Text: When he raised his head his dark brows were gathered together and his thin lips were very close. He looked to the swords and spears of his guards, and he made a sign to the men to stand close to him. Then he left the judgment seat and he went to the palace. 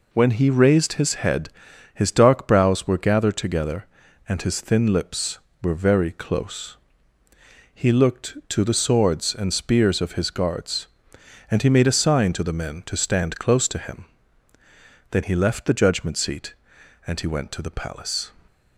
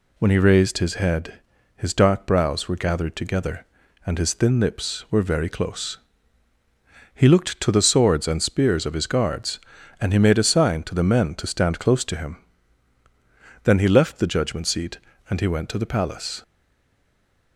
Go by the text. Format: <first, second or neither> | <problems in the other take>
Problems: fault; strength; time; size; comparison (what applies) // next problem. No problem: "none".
first | pauses between "head" and "his"; slight; at 1.4 s; 0.36 s long; also in the first // stays silent after the last word; from 16.4 s on; 1.1 s long